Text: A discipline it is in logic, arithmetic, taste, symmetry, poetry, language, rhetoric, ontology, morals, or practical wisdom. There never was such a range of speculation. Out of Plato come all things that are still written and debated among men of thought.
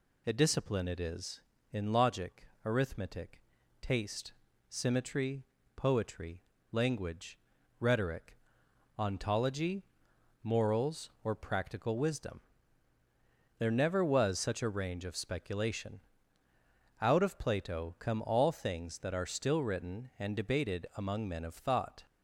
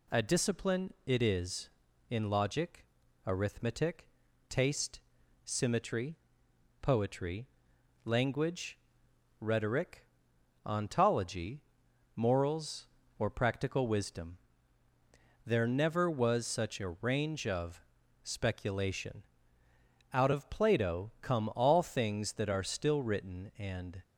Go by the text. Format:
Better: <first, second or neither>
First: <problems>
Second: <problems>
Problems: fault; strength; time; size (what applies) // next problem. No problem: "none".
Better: first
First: none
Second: pauses between "of" and "speculation"; at 17.8 s; 0.40 s long // stops before "debated among men of thought"; at 24.0 s